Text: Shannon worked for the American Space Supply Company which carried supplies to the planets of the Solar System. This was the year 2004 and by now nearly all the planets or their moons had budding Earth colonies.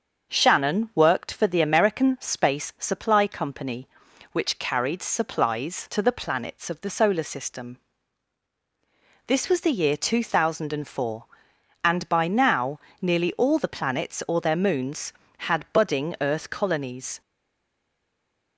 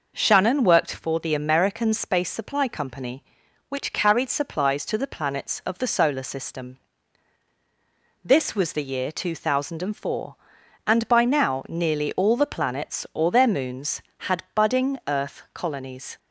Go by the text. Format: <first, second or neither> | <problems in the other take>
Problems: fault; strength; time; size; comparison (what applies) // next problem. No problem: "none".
second | starts louder than the rest; until 1.3 s; 6.5 dB // pauses between "now" and "nearly"; slight; at 12.7 s; 0.22 s long // stays silent after the last word; noticeable; from 17.2 s on; 1.3 s long